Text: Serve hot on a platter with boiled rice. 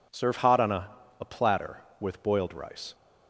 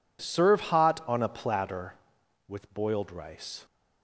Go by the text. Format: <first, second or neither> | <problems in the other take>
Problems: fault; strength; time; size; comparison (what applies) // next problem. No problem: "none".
second | says "a" twice; at 1.2 s